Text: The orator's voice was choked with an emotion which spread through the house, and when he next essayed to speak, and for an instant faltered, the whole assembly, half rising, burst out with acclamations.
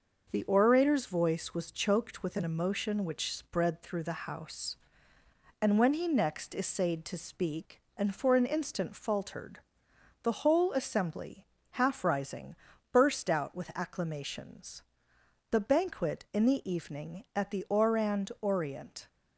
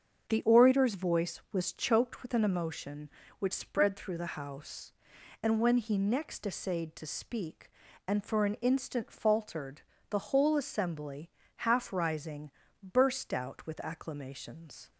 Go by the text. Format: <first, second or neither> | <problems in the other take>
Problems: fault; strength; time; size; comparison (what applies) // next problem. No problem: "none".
second | starts louder than the rest; noticeable; until 1.3 s; 6 dB; also in the second // goes on to say "The banquet in the evening at the Orand Orient"; strong; from 15.5 s on; 3.5 s long